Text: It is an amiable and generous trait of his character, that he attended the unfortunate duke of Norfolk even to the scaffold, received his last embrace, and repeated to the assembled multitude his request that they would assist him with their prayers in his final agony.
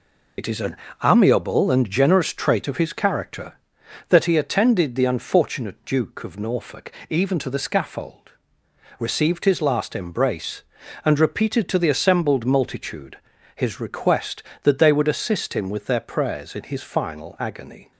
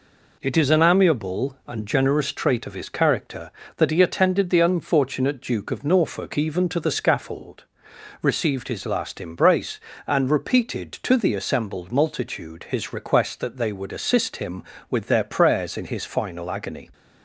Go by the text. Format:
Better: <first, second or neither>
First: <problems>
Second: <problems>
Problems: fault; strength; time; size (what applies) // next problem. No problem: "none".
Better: second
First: loses the start of "It"; at 0.3 s; 50 ms // pauses between "an" and "amiable"; slight; at 0.7 s; 0.26 s long // pauses between "Norfolk" and "even"; slight; at 6.8 s; 0.20 s long // pauses between "multitude" and "his"; at 13.1 s; 0.38 s long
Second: none